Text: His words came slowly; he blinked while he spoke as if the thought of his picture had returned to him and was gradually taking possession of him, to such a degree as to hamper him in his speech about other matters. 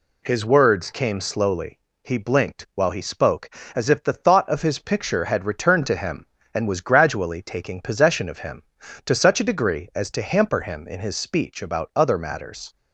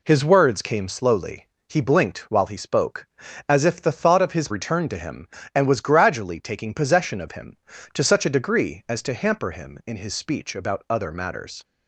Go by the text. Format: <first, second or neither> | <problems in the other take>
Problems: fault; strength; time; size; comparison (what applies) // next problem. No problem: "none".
first | skips "picture had"; at 4.4 s